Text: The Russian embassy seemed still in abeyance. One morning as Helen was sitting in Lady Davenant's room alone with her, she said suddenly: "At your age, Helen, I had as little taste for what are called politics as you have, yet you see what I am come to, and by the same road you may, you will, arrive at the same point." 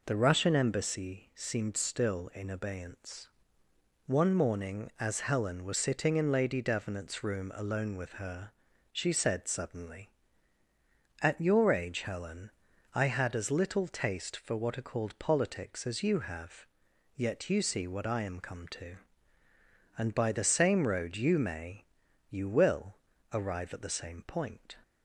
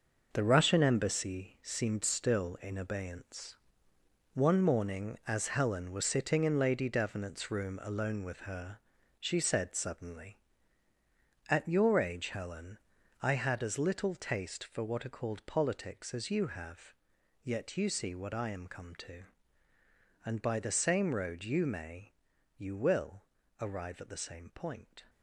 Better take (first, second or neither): first